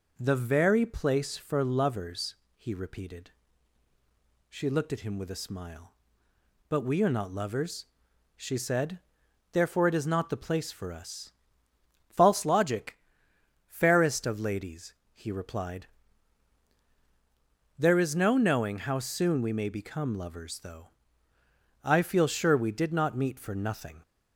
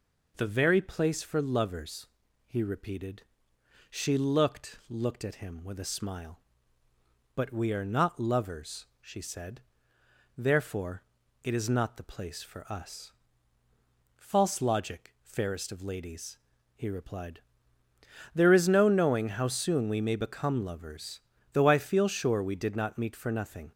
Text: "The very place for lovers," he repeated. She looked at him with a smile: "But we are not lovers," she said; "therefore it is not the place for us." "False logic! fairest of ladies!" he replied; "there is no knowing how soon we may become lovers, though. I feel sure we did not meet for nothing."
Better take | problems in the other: first | says "looked" twice; at 4.8 s // pauses between "therefore" and "it"; at 11.0 s; 0.40 s long

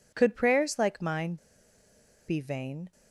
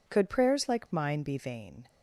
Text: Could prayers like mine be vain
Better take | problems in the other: second | pauses between "mine" and "be"; noticeable; at 1.3 s; 0.91 s long

